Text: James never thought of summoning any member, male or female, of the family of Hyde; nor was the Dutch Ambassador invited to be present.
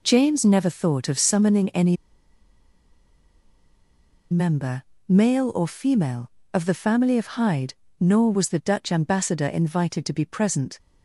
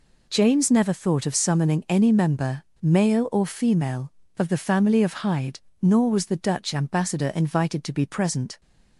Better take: second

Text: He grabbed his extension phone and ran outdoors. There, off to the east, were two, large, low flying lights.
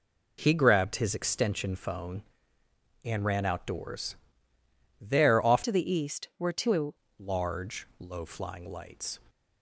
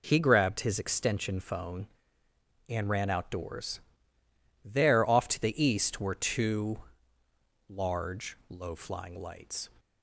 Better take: second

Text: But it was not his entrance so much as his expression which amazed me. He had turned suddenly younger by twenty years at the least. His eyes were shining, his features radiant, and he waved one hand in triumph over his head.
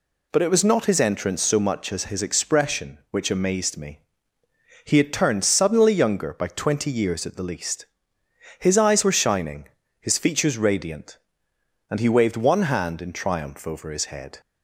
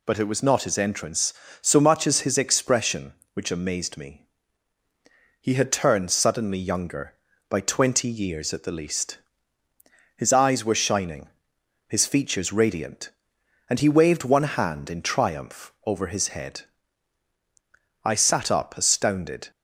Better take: first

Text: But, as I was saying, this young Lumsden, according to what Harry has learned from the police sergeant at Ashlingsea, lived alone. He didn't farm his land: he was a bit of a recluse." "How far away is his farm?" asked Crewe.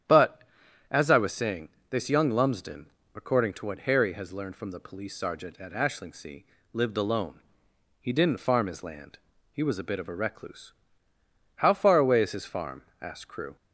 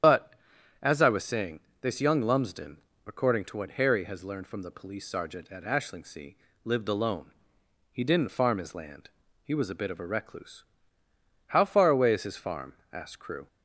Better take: first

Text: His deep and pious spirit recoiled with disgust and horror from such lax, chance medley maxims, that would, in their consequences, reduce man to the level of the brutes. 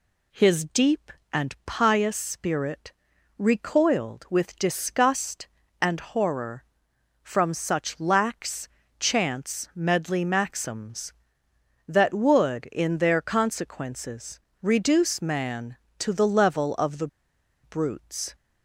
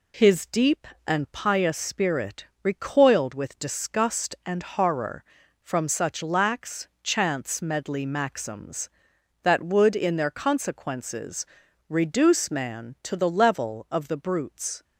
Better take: second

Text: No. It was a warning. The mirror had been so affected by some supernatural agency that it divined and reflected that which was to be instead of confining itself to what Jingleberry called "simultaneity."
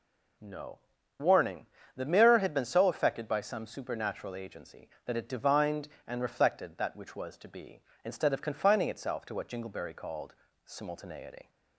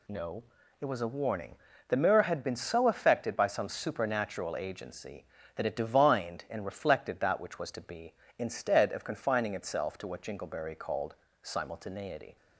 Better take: second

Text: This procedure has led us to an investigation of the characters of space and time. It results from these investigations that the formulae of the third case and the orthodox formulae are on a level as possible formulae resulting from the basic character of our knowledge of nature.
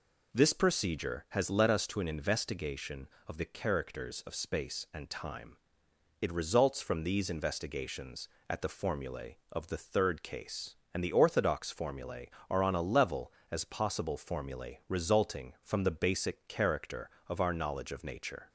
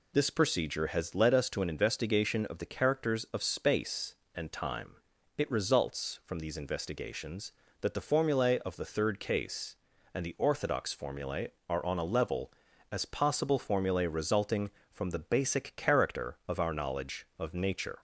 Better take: second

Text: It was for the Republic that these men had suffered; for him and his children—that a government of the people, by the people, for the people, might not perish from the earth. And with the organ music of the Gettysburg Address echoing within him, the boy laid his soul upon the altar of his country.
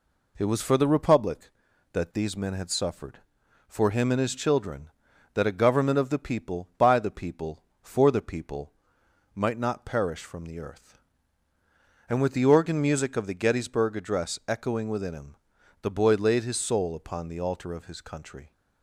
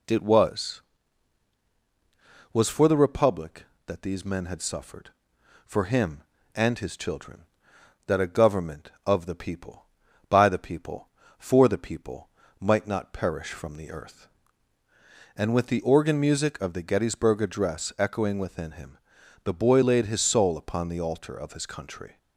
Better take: first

